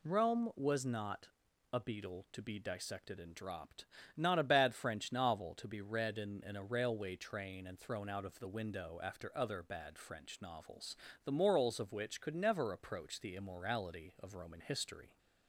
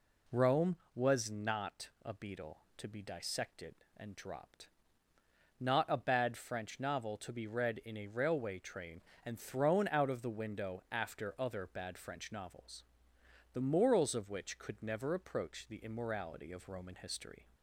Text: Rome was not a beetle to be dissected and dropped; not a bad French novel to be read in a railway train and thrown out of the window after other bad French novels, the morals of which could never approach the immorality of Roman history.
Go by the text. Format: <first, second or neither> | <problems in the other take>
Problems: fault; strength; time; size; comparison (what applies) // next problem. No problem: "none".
second | pauses between "not" and "a"; at 1.2 s; 0.44 s long; slight in the second // says "in" twice; at 6.4 s